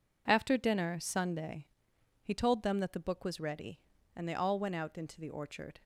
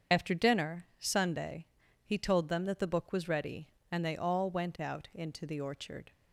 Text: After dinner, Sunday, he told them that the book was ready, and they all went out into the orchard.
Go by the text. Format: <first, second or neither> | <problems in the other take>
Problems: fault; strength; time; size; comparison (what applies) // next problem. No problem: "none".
first | loses the start of "After"; at 0.1 s; 30 ms // starts louder than the rest; strong; until 1.2 s; 7 dB